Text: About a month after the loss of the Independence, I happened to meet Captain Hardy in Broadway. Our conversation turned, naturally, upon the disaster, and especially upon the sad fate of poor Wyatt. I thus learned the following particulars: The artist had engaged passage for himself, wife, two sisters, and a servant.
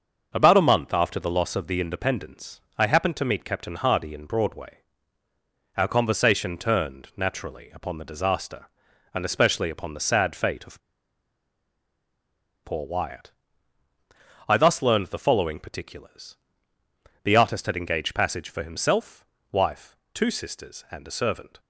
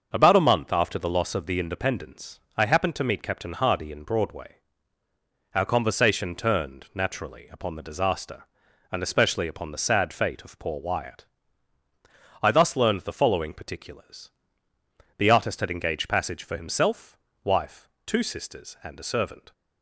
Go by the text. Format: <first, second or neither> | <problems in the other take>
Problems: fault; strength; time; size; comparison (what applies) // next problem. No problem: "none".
second | starts louder than the rest; until 1.3 s; 6.5 dB; also in the second // pauses between "of" and "poor"; strong; at 10.7 s; 1.8 s long